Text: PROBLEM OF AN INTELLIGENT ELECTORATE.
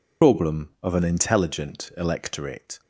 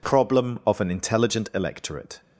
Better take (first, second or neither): second